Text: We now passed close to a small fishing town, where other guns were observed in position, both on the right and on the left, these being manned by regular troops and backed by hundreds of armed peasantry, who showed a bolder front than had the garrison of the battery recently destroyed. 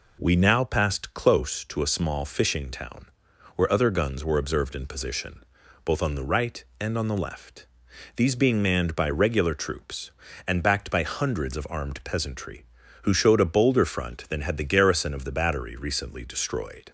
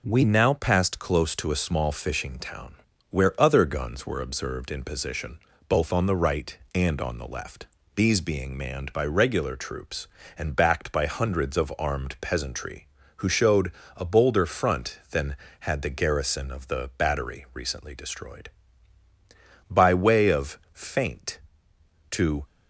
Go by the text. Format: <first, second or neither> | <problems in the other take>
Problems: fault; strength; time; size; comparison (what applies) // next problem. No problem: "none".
first | pauses between "showed" and "a"; slight; at 13.7 s; 0.26 s long // goes on to say "By way of feint to"; strong; from 19.7 s on; 2.7 s long